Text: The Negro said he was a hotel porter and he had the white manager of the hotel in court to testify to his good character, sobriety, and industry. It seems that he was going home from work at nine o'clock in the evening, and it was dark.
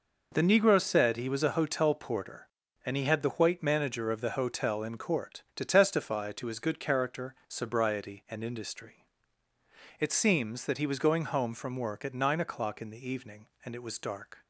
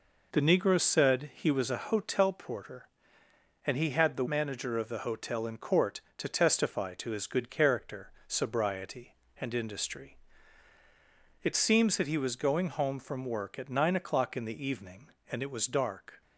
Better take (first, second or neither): first